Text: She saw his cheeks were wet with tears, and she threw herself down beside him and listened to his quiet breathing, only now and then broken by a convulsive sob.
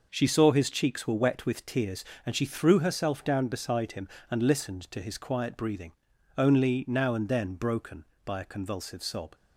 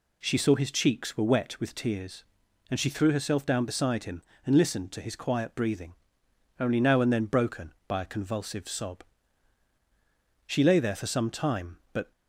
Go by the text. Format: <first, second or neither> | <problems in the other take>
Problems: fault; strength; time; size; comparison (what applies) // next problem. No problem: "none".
first | goes on to say "She lay there for some time but"; from 10.4 s on; 1.6 s long